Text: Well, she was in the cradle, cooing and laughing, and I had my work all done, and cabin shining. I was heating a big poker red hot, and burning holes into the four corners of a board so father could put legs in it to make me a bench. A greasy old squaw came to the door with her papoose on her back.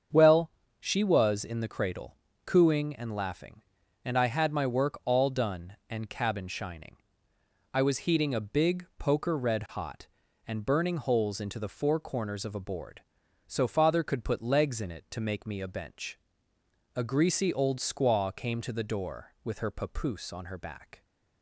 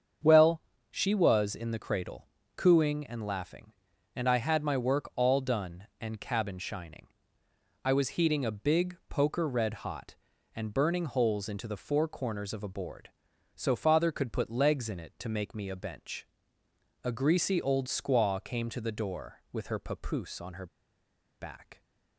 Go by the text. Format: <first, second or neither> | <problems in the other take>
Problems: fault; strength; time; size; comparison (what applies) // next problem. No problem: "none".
first | starts louder than the rest; strong; until 1.5 s; 7.5 dB; strong in the first // pauses between "her" and "back"; noticeable; at 20.6 s; 0.72 s long